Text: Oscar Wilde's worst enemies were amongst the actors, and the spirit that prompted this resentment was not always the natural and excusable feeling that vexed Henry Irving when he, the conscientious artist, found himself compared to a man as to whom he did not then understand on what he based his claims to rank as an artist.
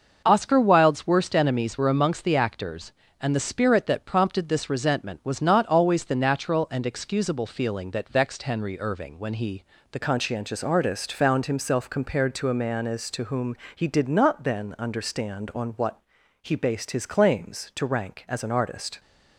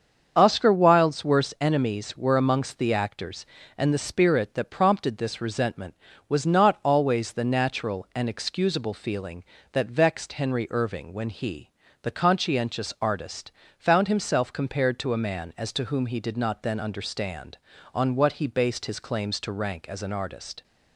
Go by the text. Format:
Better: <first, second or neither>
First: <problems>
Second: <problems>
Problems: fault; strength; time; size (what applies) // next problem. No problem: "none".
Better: second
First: starts louder than the rest; noticeable; until 1.2 s; 6 dB // changes voice at "conscientious"; from 10.0 s on; 8.9 s long // pauses between "whom" and "he"; slight; at 13.5 s; 0.18 s long // pauses between "what" and "he"; at 16.0 s; 0.40 s long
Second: starts louder than the rest; until 1.3 s; 7 dB